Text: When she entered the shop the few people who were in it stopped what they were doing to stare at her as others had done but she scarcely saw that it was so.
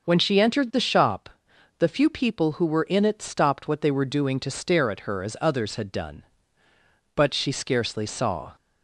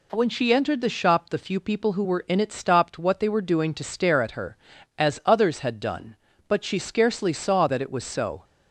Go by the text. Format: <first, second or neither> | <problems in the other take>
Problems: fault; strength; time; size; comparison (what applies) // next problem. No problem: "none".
second | pauses between "shop" and "the"; noticeable; at 1.2 s; 0.50 s long // stops before "that it was so"; at 8.5 s